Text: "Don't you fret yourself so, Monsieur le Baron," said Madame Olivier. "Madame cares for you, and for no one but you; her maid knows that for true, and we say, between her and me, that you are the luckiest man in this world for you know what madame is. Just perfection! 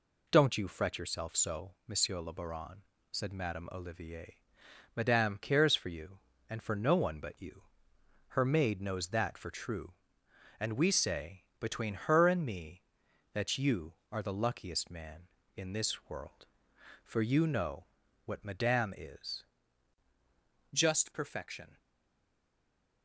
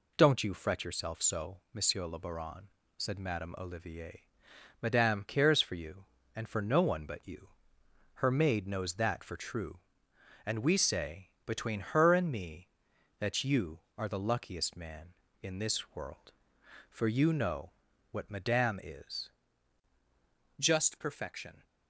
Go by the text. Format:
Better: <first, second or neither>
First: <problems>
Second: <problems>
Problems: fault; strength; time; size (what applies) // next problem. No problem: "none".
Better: second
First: pauses between "know" and "what"; at 17.8 s; 0.40 s long // stays silent after the last word; noticeable; from 21.7 s on; 1.3 s long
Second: pauses between "know" and "what"; at 17.7 s; 0.40 s long